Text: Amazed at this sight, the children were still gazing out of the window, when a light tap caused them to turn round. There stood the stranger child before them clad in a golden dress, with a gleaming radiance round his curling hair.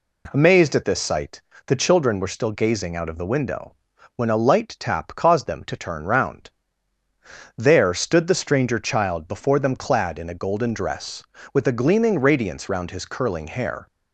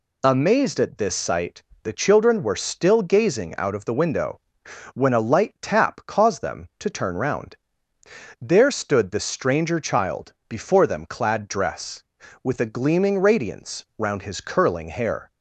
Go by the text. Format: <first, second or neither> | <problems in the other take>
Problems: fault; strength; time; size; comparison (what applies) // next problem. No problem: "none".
first | pauses between "child" and "before"; slight; at 10.3 s; 0.16 s long // skips "in a golden"; at 11.4 s